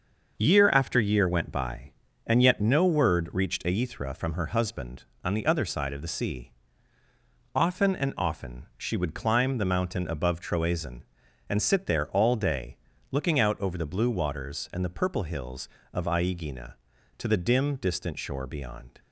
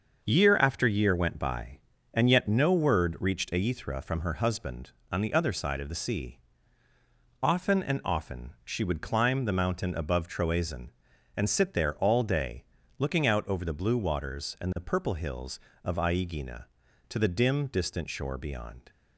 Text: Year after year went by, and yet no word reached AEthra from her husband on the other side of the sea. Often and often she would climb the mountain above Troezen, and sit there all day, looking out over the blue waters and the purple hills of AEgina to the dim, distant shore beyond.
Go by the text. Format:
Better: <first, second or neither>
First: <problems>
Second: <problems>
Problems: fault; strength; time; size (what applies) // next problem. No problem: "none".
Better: neither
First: starts louder than the rest; until 1.3 s; 6.5 dB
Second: starts louder than the rest; until 1.2 s; 6.5 dB